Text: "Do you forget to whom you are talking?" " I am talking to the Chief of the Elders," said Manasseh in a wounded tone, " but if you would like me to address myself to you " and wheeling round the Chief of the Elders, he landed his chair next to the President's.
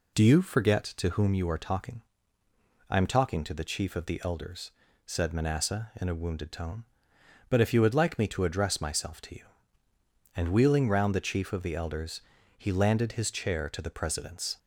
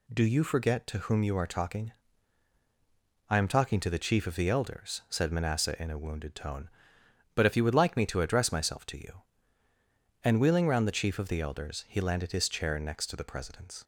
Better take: second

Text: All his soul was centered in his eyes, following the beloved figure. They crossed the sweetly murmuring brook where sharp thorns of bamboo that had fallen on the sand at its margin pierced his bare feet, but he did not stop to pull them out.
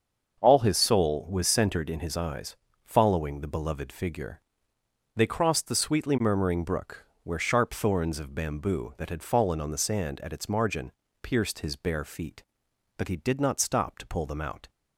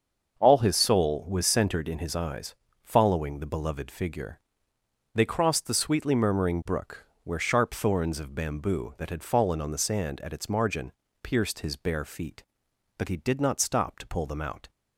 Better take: neither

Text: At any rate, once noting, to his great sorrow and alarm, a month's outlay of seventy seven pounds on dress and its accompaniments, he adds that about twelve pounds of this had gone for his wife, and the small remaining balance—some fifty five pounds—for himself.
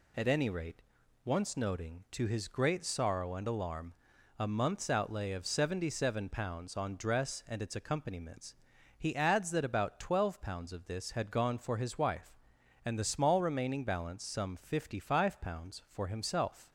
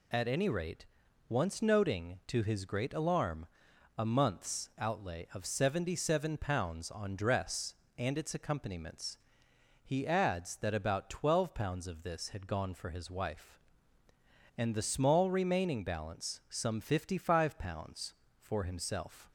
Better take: first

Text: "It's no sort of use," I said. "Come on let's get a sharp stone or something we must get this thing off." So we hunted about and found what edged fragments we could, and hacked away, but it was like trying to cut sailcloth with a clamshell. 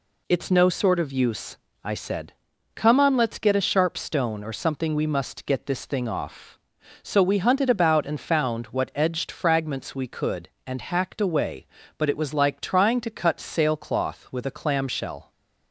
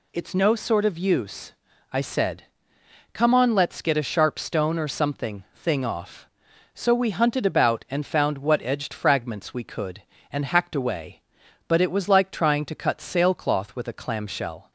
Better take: first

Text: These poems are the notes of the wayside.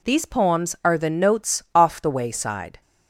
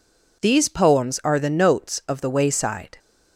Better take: second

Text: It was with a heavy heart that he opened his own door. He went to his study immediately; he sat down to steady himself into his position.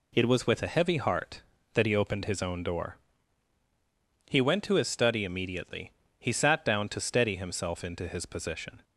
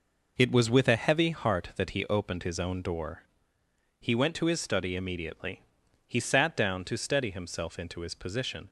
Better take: neither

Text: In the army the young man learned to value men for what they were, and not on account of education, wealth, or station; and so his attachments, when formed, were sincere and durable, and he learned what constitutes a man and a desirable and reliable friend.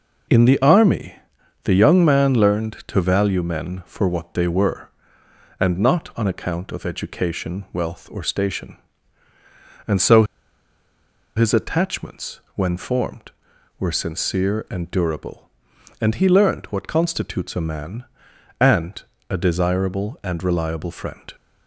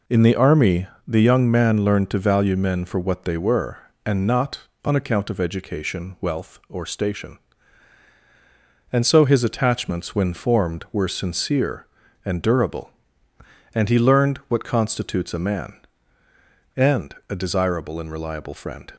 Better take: second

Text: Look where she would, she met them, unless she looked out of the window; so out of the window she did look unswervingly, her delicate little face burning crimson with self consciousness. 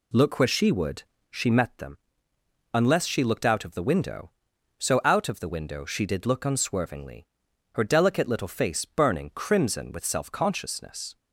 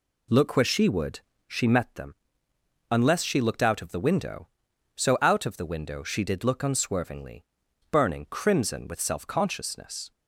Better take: first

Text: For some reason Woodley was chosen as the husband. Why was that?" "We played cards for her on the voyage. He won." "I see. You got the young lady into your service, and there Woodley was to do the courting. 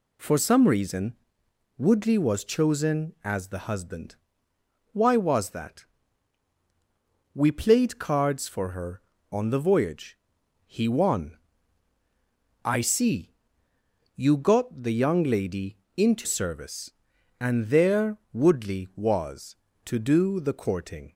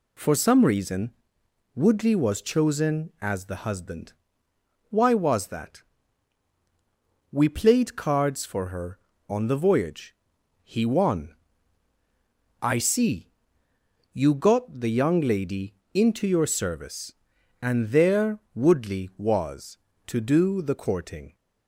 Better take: second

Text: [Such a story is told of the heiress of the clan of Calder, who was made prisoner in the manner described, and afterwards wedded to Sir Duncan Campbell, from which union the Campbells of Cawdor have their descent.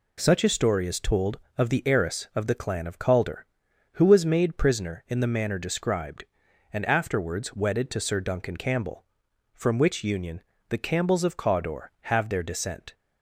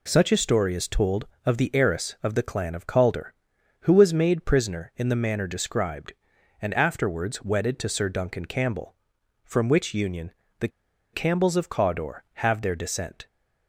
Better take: first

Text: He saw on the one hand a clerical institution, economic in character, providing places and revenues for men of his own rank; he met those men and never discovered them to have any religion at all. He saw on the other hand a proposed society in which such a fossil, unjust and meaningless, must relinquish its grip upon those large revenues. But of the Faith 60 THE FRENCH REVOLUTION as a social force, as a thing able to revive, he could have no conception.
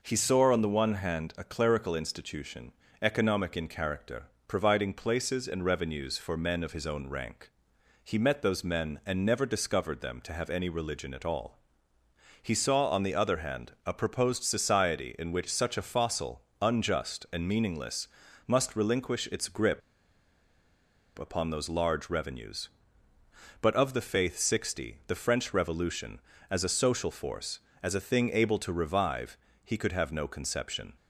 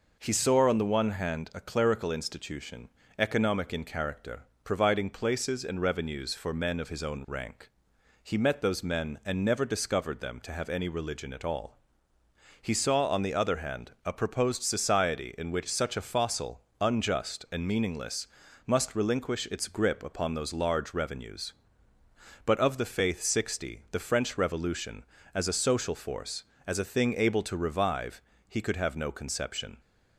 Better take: second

